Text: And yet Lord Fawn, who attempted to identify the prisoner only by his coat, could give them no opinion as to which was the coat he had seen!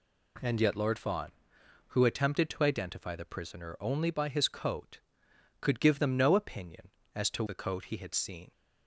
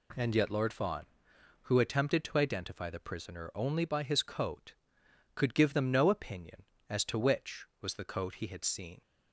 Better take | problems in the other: second | skips "which was"; at 7.4 s

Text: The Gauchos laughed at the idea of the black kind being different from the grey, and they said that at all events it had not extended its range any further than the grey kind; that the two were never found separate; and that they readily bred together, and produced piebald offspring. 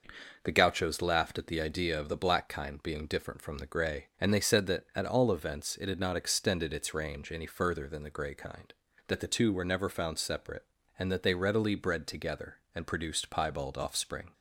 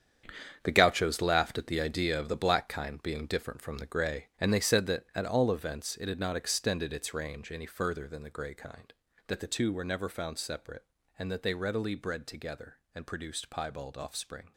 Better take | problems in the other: first | gets quieter; strong; throughout; 11.5 dB

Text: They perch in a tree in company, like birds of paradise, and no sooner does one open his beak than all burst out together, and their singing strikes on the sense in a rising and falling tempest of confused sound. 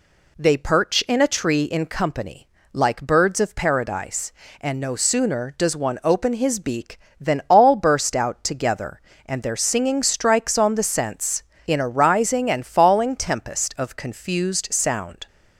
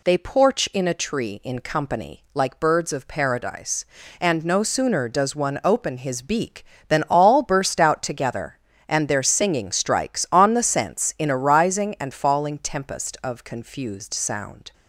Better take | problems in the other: first | says "porch" for "perch"; at 0.1 s

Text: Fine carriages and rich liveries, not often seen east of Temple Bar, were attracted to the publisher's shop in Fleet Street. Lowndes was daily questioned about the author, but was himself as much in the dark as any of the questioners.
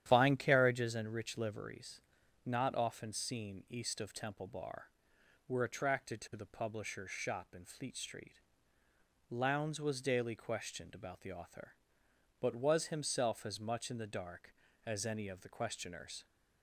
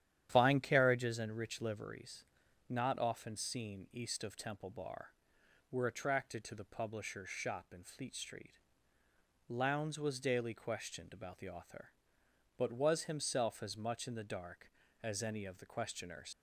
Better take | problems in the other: first | starts louder than the rest; strong; until 1.3 s; 10.5 dB; strong in the first // leaves "questioners" unfinished; at 16.3 s; 95 ms

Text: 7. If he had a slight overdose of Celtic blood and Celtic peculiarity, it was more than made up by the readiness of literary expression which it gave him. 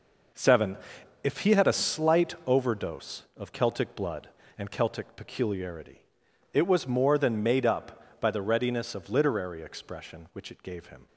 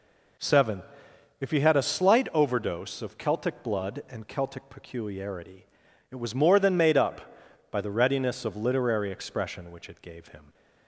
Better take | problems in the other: second | gets quieter; strong; throughout; 10 dB

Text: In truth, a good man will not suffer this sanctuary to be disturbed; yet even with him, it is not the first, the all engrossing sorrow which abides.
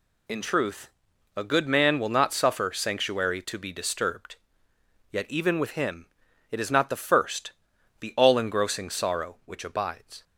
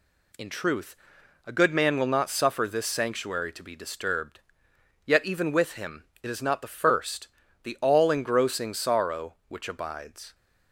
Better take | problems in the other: second | skips "this"; at 2.7 s

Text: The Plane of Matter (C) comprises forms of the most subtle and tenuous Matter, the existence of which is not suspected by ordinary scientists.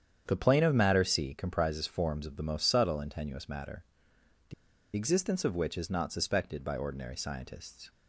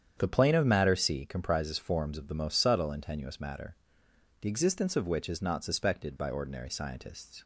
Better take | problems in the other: second | starts louder than the rest; strong; until 1.2 s; 8.5 dB; strong in the second // pauses between "the" and "existence"; at 4.5 s; 0.42 s long

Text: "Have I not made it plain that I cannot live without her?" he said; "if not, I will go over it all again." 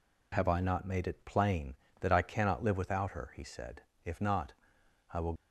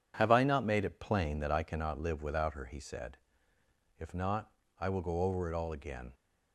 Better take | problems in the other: second | stops before "go over it all again"; at 5.3 s

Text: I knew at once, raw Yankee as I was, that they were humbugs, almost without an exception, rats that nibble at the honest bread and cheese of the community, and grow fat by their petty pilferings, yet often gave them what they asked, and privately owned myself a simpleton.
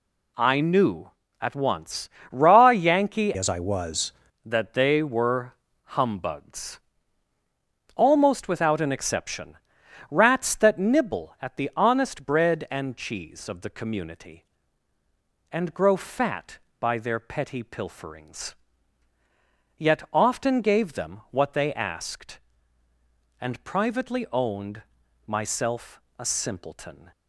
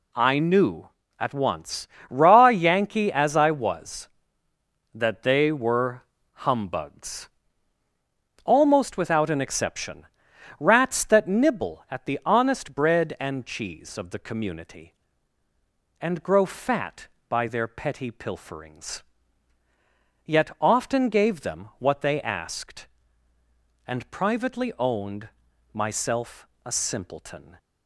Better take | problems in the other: second | changes voice from "as" to "was"; from 3.3 to 4.1 s; 0.8 s long // pauses between "were" and "humbugs"; slight; at 5.5 s; 0.30 s long; slight in the second // pauses between "owned" and "myself"; noticeable; at 24.8 s; 0.46 s long; noticeable in the second // pauses between "myself" and "a"; slight; at 26.0 s; 0.16 s long; slight in the second

